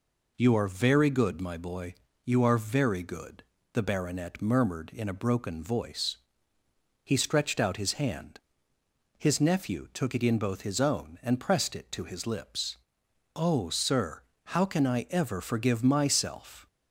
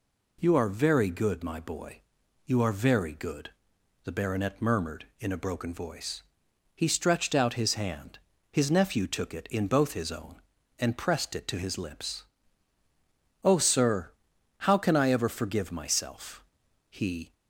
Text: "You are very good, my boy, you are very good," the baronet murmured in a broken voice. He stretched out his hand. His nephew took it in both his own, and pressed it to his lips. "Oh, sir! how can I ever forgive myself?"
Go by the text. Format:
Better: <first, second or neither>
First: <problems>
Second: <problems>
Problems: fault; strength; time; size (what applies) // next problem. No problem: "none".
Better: first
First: none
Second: goes on to say "he"; slight; from 16.8 s on; 0.44 s long